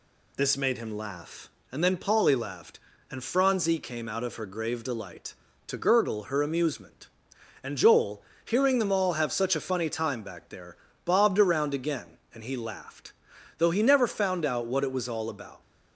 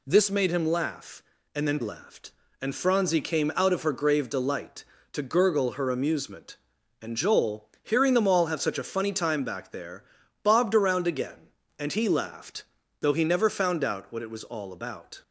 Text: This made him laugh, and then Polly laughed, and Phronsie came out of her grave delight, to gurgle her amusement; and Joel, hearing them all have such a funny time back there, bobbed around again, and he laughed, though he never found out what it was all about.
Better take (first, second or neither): first